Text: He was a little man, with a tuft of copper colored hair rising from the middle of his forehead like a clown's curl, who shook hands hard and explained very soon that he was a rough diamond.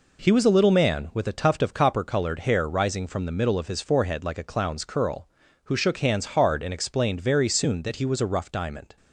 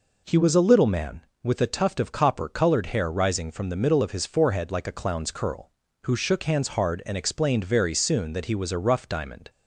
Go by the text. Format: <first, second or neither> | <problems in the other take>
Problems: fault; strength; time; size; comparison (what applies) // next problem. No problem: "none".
neither | none